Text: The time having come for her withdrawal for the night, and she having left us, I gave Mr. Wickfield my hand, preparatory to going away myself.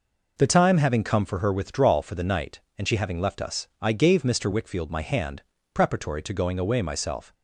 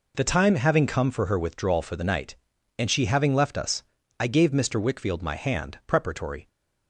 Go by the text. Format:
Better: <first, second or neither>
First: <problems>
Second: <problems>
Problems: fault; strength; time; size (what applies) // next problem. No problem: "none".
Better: first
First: none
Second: stops before "to going away myself"; at 6.4 s